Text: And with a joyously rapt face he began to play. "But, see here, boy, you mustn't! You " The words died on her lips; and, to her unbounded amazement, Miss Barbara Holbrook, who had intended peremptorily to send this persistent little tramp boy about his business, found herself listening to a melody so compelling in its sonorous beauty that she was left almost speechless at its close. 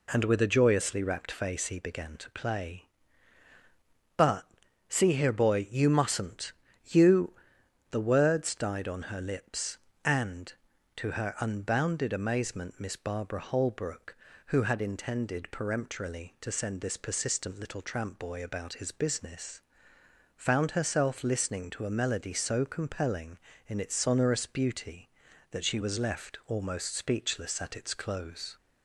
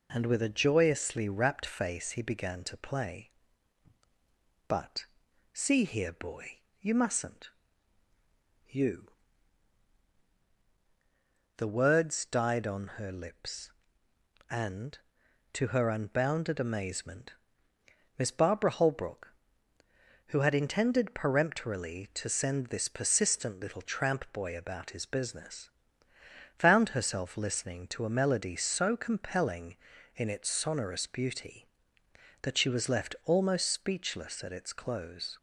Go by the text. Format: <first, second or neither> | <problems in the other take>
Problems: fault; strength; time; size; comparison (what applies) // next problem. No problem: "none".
neither | none